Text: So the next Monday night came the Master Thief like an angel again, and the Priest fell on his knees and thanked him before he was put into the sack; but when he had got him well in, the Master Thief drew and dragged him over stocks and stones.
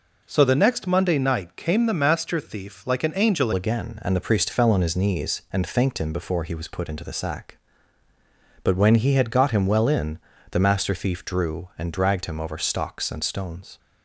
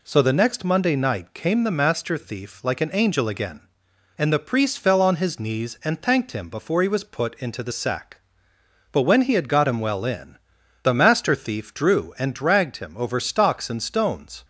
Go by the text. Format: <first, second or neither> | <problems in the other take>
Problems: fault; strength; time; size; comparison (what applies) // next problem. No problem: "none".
second | changes voice at "again"; from 3.5 s on; 10.2 s long